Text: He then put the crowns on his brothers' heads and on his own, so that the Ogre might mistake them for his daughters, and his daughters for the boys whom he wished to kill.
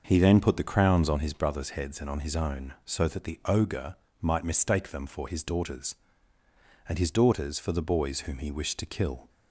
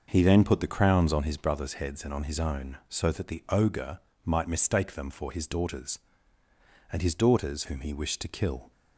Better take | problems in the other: first | starts louder than the rest; noticeable; until 1.0 s; 6 dB; noticeable in the first // pauses between "Ogre" and "might"; slight; at 3.9 s; 0.26 s long; slight in the first // skips "for the boys"; at 7.6 s

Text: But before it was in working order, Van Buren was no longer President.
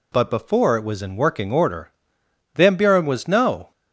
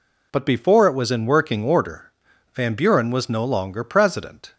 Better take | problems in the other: second | stops before "longer President"; at 3.7 s

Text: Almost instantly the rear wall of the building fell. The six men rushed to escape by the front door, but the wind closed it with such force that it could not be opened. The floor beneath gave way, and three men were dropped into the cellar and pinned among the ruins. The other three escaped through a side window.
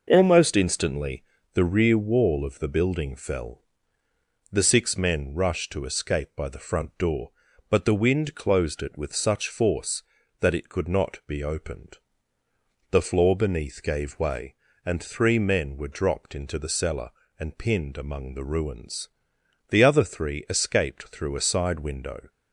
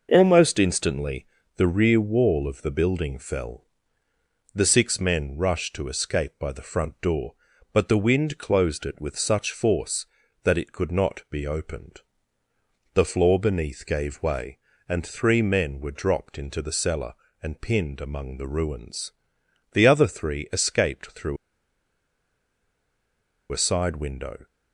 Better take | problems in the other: first | pauses between "instantly" and "the"; slight; at 1.2 s; 0.30 s long; slight in the first // pauses between "through" and "a"; strong; at 21.3 s; 2.1 s long

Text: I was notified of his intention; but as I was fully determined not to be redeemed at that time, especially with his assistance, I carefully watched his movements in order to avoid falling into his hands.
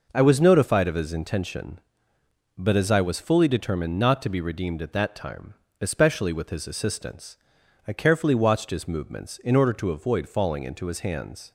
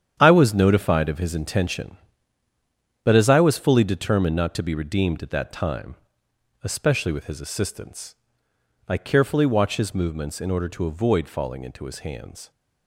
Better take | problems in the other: first | gets quieter; strong; throughout; 10 dB

